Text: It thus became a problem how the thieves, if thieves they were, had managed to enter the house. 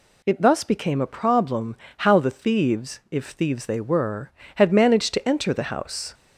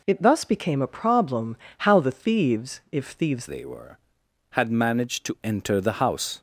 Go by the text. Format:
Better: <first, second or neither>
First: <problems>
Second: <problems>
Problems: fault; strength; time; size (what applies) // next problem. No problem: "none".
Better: first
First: pauses between "problem" and "how"; slight; at 1.7 s; 0.24 s long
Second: pauses between "problem" and "how"; slight; at 1.5 s; 0.24 s long // changes voice at "they"; from 3.4 s on; 3.0 s long